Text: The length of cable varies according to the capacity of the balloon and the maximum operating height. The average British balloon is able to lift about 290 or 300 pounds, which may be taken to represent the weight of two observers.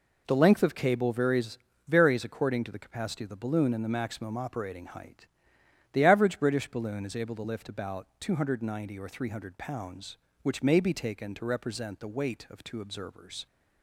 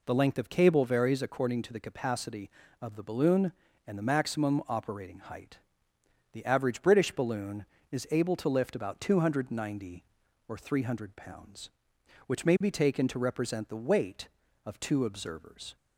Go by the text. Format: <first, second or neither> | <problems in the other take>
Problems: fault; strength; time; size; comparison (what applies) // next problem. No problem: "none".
second | says "varies" twice; at 1.8 s